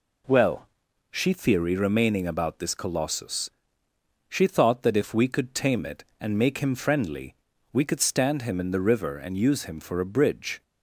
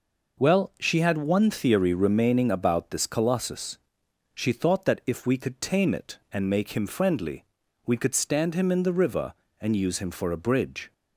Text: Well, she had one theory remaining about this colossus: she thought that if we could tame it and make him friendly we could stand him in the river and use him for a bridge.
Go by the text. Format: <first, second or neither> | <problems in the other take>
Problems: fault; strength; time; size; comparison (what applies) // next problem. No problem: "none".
second | skips "had one"; at 1.3 s // pauses between "friendly" and "we"; at 7.3 s; 0.40 s long; also in the second